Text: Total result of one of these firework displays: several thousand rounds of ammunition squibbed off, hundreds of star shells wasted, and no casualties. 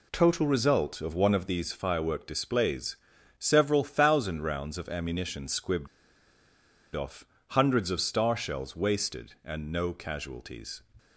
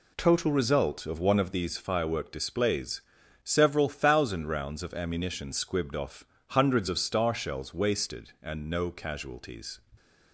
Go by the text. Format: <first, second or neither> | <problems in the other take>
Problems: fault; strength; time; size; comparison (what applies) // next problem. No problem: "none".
second | pauses between "squibbed" and "off"; at 5.8 s; 1.0 s long